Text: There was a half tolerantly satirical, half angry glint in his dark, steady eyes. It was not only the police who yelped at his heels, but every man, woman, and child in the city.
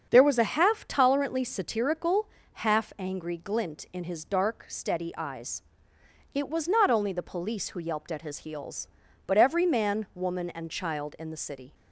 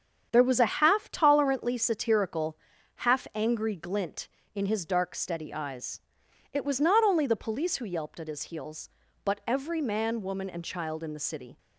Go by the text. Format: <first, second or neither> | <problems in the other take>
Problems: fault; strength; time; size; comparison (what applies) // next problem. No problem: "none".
neither | starts louder than the rest; the same in both